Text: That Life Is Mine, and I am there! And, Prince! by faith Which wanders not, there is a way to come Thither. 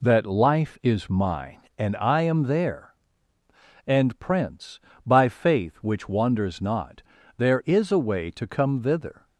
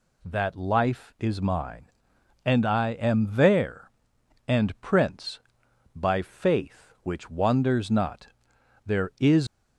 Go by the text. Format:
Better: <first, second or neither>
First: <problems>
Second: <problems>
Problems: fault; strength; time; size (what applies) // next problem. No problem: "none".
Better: first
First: none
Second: stops before "a way to come Thither"; at 9.4 s